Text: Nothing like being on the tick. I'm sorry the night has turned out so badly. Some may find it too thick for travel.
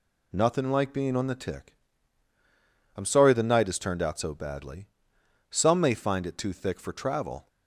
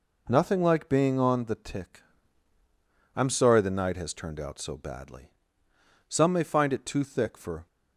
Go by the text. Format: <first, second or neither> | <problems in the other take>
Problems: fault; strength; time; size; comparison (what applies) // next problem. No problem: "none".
first | stops before "travel"; at 7.6 s